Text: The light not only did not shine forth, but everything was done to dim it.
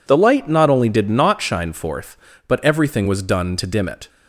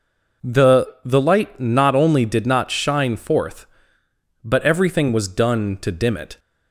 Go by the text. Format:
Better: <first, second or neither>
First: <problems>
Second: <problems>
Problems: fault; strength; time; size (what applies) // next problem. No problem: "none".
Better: first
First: none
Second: says "The" twice; at 1.0 s